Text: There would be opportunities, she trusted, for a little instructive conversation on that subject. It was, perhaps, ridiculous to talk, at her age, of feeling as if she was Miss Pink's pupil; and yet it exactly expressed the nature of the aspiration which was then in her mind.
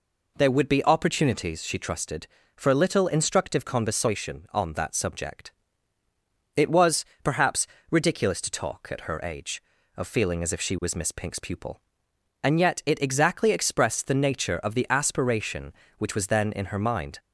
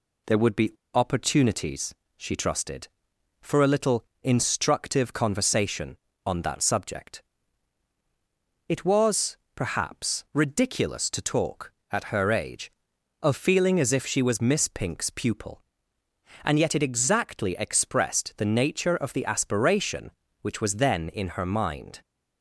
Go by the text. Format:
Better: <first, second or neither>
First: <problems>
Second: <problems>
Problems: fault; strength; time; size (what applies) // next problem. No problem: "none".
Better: first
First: none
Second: pauses between "be" and "opportunities"; slight; at 0.7 s; 0.21 s long // pauses between "little" and "instructive"; slight; at 4.0 s; 0.20 s long